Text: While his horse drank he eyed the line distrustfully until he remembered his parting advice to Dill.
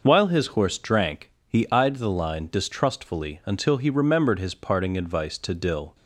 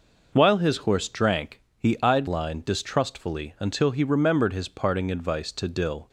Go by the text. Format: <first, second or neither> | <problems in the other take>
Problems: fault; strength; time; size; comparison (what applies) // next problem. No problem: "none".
first | pauses between "drank" and "he"; slight; at 1.6 s; 0.16 s long; slight in the first // skips "the"; at 2.2 s